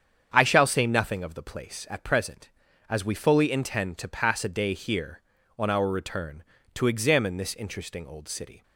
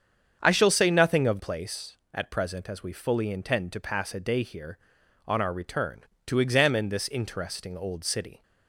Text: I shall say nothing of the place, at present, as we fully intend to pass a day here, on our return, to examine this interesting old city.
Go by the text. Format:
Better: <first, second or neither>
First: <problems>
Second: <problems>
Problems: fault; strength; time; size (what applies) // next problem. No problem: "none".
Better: first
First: starts louder than the rest; strong; until 1.3 s; 7.5 dB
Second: starts louder than the rest; strong; until 1.4 s; 7.5 dB // skips "the"; at 1.3 s